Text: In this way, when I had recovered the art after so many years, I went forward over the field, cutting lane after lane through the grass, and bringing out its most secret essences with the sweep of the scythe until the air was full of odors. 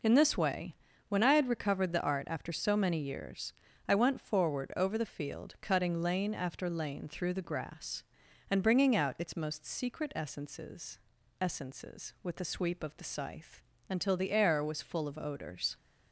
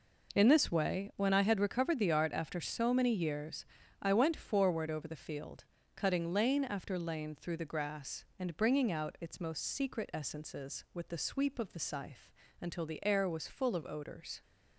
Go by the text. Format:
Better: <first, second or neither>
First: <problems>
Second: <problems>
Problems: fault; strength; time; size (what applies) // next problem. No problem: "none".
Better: second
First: says "essences" twice; at 11.3 s // pauses between "scythe" and "until"; slight; at 13.6 s; 0.26 s long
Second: pauses between "scythe" and "until"; slight; at 12.3 s; 0.30 s long